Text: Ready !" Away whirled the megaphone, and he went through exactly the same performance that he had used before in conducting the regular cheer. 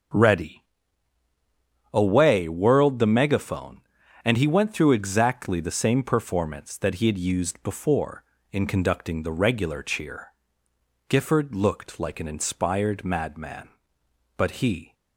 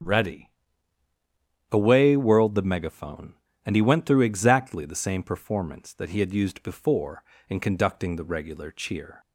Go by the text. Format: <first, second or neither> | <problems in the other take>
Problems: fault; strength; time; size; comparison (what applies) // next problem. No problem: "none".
second | goes on to say "Gifford looked like an inspired madman but he"; strong; from 11.0 s on; 3.8 s long